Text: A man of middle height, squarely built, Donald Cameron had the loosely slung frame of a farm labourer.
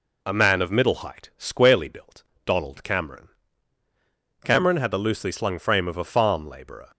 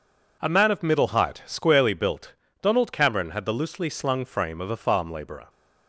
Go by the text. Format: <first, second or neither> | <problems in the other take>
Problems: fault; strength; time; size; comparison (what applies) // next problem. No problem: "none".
second | says "Cameron" twice; at 4.4 s